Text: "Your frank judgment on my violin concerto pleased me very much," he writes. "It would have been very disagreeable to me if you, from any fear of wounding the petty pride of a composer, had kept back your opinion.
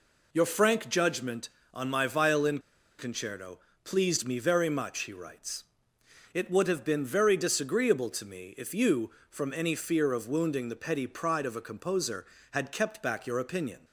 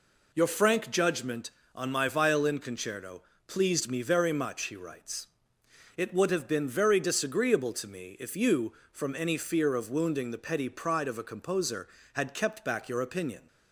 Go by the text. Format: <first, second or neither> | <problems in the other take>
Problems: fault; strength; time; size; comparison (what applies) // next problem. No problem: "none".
second | pauses between "violin" and "concerto"; at 2.5 s; 0.39 s long // pauses between "concerto" and "pleased"; slight; at 3.5 s; 0.28 s long; slight in the second